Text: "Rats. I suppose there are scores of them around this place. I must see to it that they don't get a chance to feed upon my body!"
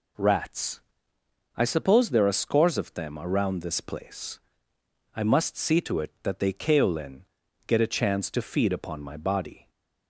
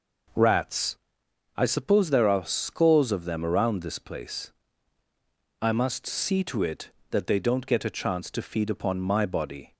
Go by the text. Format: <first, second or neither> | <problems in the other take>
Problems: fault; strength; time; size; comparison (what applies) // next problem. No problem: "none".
second | says "kaolin" for "don't"; at 6.5 s